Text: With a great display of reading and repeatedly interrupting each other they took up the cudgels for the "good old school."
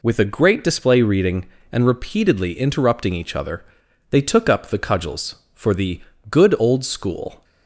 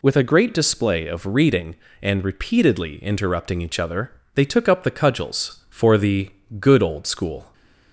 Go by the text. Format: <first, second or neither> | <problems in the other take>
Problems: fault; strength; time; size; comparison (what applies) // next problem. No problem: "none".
second | skips "of"; at 1.0 s // pauses between "other" and "they"; noticeable; at 3.6 s; 0.46 s long; slight in the second // pauses between "the" and "good"; slight; at 6.0 s; 0.28 s long; slight in the second